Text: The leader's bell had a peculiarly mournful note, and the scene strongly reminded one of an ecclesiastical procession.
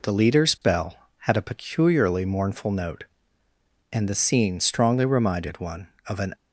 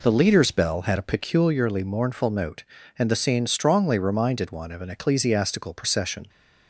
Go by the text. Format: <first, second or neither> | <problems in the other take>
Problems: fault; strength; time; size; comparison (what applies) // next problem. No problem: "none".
second | stops before "ecclesiastical procession"; at 6.3 s